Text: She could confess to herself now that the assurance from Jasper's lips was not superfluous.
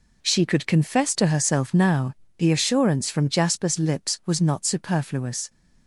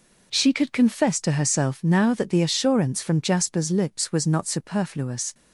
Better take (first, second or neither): second